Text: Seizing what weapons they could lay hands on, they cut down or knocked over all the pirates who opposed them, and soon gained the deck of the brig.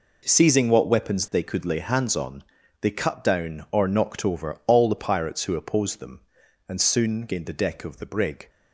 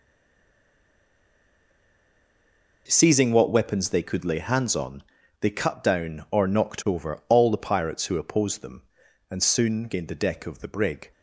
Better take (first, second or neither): first